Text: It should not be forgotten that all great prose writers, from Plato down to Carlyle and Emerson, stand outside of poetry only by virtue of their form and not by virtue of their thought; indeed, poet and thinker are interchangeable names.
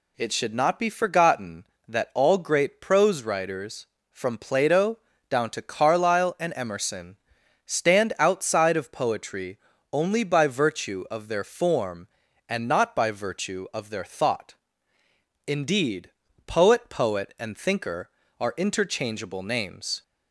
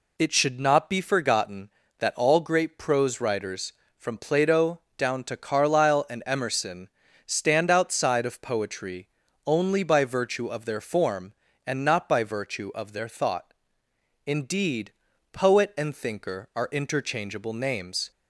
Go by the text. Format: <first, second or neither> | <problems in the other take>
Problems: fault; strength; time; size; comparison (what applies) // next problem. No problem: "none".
second | pauses between "Plato" and "down"; slight; at 4.9 s; 0.30 s long; slight in the second // pauses between "poetry" and "only"; slight; at 9.5 s; 0.34 s long; also in the second // says "poet" twice; at 16.8 s